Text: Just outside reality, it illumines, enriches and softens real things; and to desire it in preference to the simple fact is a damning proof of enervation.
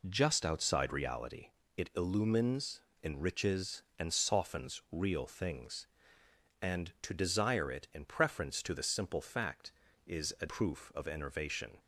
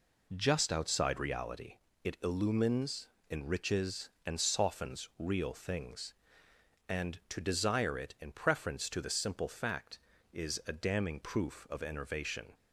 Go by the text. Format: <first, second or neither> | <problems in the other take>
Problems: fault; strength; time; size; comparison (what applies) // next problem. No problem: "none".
second | skips "damning"; at 10.4 s